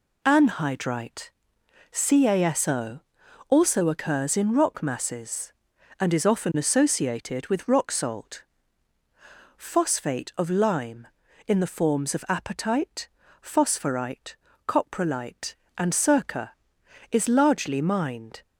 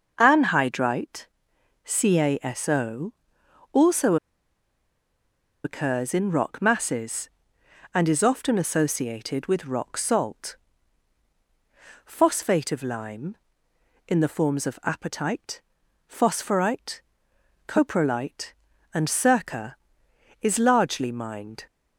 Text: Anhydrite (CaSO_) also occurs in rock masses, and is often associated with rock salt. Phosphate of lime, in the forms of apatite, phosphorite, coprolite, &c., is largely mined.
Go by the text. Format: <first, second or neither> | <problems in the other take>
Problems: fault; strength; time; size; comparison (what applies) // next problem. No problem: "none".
first | starts louder than the rest; noticeable; until 1.1 s; 6 dB // pauses between "also" and "occurs"; strong; at 4.1 s; 1.4 s long